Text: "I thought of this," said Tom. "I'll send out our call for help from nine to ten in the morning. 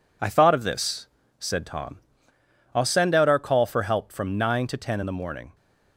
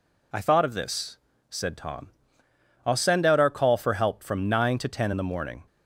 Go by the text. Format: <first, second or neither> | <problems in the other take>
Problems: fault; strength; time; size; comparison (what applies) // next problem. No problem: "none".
second | gets quieter; noticeable; throughout; 6 dB